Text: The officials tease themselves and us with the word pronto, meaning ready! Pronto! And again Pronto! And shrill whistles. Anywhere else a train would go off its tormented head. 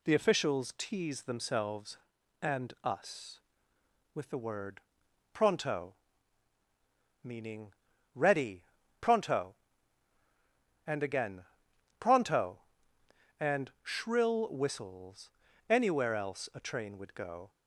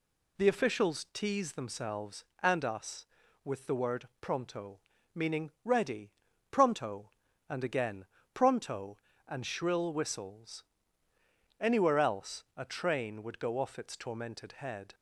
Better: second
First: pauses between "word" and "pronto"; noticeable; at 4.7 s; 0.52 s long // pauses between "meaning" and "ready"; noticeable; at 7.6 s; 0.46 s long // pauses between "again" and "Pronto"; noticeable; at 11.4 s; 0.54 s long // stops before "off its tormented head"; at 17.5 s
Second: pauses between "again" and "Pronto"; slight; at 8.0 s; 0.28 s long

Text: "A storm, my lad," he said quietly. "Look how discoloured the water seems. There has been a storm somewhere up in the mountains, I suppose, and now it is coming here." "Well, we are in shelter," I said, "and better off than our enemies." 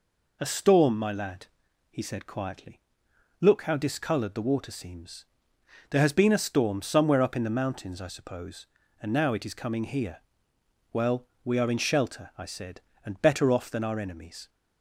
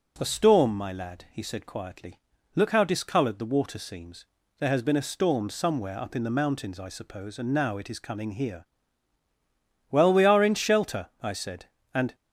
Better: first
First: none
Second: stops before "better off than our enemies"; at 12.1 s

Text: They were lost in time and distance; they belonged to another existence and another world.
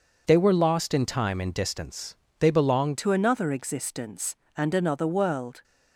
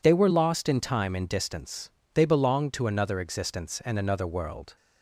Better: second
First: changes voice at "to"; from 2.9 s on; 2.7 s long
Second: none

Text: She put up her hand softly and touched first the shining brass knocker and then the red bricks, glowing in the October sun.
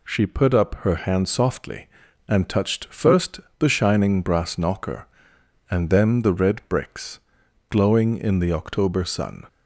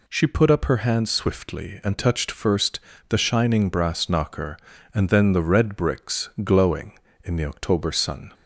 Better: first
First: pauses between "first" and "the"; slight; at 3.4 s; 0.18 s long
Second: says "swiftly" for "softly"; at 1.0 s // pauses between "first" and "the"; slight; at 2.7 s; 0.30 s long

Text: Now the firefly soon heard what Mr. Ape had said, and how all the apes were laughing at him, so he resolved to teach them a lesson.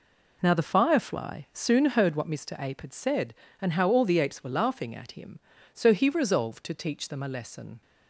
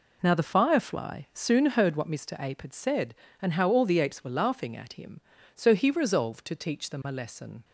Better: neither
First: none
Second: none

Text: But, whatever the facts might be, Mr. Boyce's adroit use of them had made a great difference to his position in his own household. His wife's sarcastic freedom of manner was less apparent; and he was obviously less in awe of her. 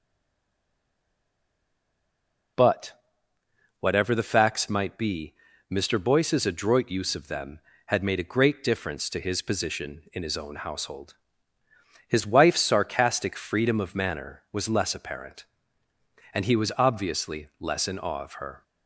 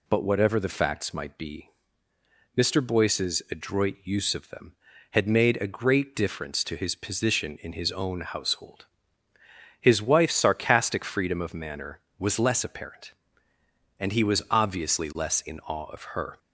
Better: second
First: stays silent before the first word; strong; until 2.5 s; 2.5 s long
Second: none

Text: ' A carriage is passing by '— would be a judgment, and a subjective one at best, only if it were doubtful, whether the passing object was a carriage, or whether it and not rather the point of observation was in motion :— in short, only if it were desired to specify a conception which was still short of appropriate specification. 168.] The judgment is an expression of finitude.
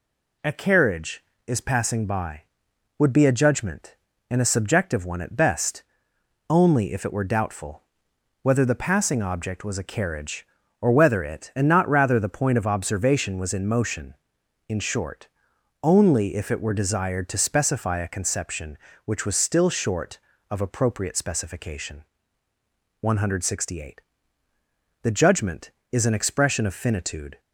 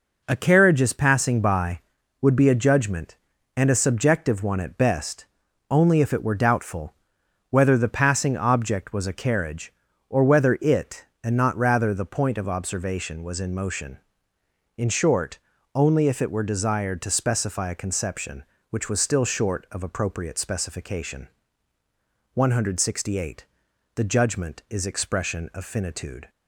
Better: first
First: none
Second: skips "an"; at 24.8 s

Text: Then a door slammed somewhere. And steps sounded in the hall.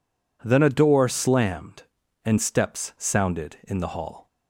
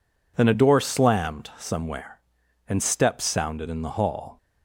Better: second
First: skips "somewhere"; at 2.0 s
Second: none

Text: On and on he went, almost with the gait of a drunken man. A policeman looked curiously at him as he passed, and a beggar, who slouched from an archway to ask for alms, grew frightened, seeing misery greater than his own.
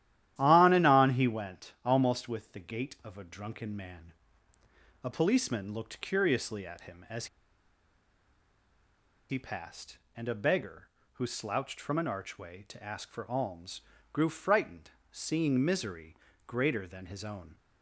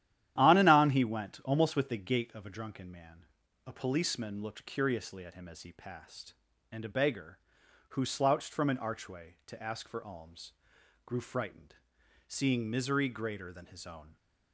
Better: second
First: starts louder than the rest; strong; until 1.3 s; 12.5 dB // pauses between "as" and "he"; strong; at 7.2 s; 2.0 s long // pauses between "misery" and "greater"; slight; at 16.1 s; 0.32 s long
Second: starts louder than the rest; strong; until 1.3 s; 11.5 dB

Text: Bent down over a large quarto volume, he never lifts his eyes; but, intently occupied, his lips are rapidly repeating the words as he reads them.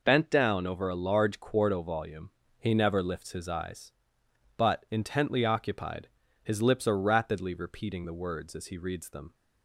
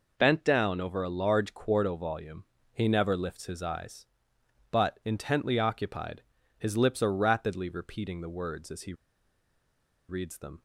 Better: first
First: none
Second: pauses between "he" and "reads"; at 8.9 s; 1.1 s long

